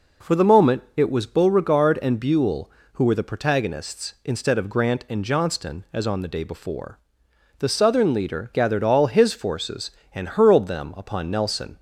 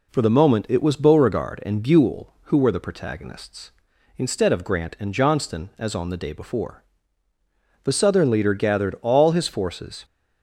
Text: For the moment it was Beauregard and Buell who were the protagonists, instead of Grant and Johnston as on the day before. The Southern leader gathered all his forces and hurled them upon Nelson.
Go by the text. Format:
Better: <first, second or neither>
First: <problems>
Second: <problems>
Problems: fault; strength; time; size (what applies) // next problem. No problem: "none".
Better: first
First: none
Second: stops before "and hurled them upon Nelson"; at 10.0 s